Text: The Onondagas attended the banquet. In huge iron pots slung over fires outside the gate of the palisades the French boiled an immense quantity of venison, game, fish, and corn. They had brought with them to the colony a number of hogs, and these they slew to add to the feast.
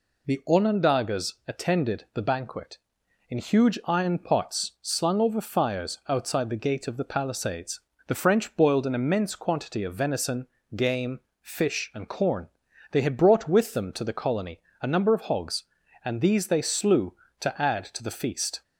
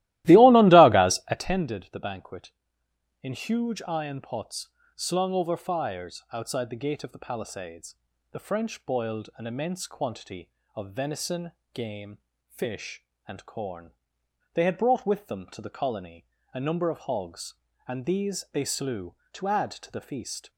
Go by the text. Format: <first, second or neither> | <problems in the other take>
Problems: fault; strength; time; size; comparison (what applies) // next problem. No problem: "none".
first | starts louder than the rest; strong; until 1.4 s; 16.5 dB // pauses between "pots" and "slung"; slight; at 4.6 s; 0.26 s long // pauses between "palisades" and "the"; at 7.9 s; 0.38 s long; slight in the first // pauses between "colony" and "a"; slight; at 16.2 s; 0.26 s long; slight in the first